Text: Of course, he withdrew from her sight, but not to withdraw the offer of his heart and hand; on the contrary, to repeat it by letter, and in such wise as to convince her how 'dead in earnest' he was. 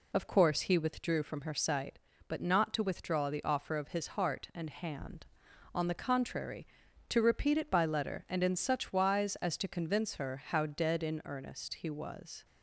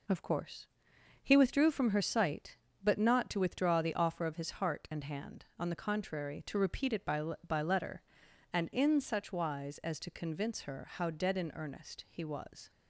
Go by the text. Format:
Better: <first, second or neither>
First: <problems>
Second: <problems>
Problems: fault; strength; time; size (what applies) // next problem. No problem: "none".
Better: first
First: none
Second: says "by" twice; at 7.4 s